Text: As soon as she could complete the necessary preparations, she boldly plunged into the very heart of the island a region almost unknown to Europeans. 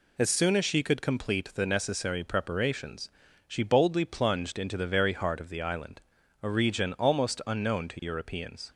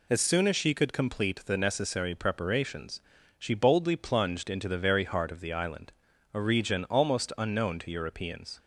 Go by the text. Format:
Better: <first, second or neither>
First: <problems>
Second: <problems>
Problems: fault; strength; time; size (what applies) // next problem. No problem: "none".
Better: neither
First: pauses between "island" and "a"; at 6.0 s; 0.40 s long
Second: pauses between "island" and "a"; at 5.9 s; 0.40 s long